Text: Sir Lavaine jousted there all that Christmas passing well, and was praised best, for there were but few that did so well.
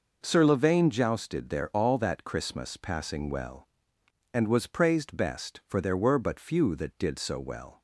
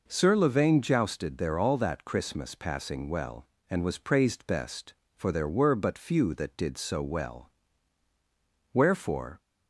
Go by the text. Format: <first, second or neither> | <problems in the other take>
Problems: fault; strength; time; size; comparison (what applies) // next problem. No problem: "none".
first | goes on to say "Wherefore"; noticeable; from 8.7 s on; 0.68 s long